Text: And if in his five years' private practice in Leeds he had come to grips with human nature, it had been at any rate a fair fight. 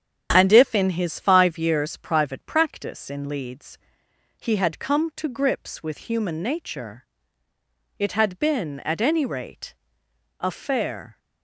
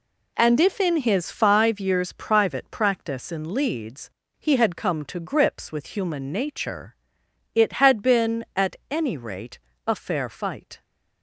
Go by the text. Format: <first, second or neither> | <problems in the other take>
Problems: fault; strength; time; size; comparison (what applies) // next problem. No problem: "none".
second | starts louder than the rest; strong; until 1.3 s; 8.5 dB // pauses between "Leeds" and "he"; noticeable; at 3.7 s; 0.62 s long; slight in the second // pauses between "rate" and "a"; noticeable; at 9.7 s; 0.66 s long; slight in the second // stops before "fight"; at 11.1 s